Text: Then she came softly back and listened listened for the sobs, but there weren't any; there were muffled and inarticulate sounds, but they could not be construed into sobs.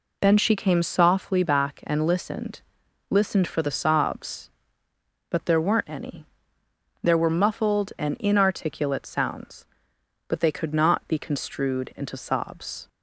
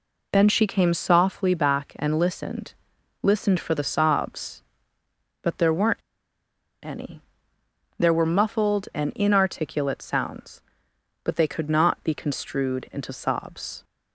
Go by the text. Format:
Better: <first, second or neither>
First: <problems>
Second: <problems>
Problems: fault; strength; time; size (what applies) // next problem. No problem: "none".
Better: first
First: pauses between "listened" and "listened"; noticeable; at 2.6 s; 0.46 s long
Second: pauses between "listened" and "listened"; noticeable; at 2.7 s; 0.46 s long // pauses between "weren't" and "any"; noticeable; at 6.0 s; 0.84 s long